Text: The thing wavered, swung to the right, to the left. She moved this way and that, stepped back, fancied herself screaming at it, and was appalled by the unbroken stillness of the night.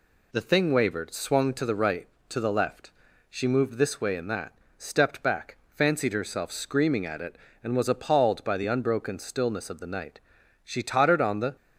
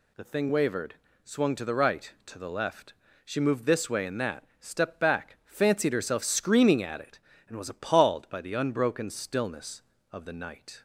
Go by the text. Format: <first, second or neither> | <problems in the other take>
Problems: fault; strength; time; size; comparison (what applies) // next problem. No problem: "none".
second | goes on to say "She tottered on the"; noticeable; from 10.6 s on; 0.92 s long